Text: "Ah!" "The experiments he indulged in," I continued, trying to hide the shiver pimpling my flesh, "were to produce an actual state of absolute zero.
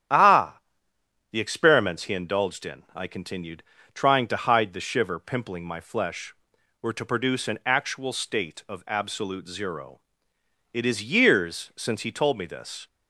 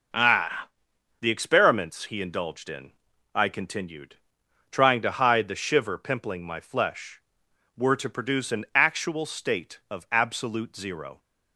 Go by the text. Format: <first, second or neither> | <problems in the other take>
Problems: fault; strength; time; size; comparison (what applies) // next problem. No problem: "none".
second | starts louder than the rest; strong; until 1.8 s; 10 dB // goes on to say "It is years since he told me this"; strong; from 10.7 s on; 2.1 s long